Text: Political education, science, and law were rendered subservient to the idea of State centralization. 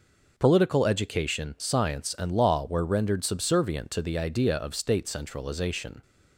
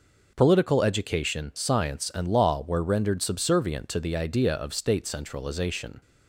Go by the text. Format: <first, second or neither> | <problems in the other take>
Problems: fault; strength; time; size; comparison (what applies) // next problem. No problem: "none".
neither | none